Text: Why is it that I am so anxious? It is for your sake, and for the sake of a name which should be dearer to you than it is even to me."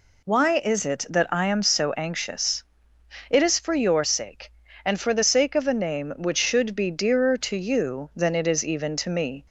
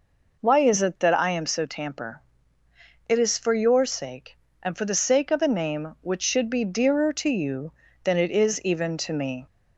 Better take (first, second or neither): first